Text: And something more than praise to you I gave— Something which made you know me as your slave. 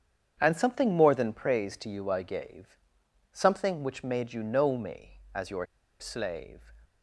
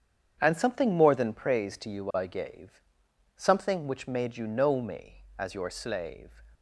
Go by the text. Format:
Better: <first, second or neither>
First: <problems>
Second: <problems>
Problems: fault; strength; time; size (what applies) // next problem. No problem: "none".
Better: second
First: starts louder than the rest; strong; until 1.4 s; 8 dB // pauses between "your" and "slave"; slight; at 5.6 s; 0.34 s long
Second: starts louder than the rest; strong; until 1.4 s; 8 dB